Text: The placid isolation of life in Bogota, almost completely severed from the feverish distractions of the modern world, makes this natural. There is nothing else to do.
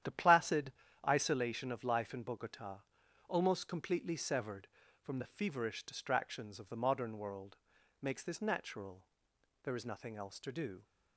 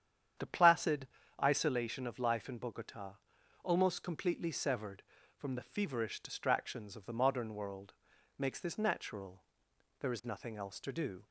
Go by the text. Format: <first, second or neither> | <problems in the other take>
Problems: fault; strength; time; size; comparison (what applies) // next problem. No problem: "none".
second | gets quieter; strong; throughout; 8.5 dB // starts louder than the rest; strong; until 1.3 s; 10.5 dB; strong in the second // pauses between "placid" and "isolation"; slight; at 0.7 s; 0.34 s long; slight in the second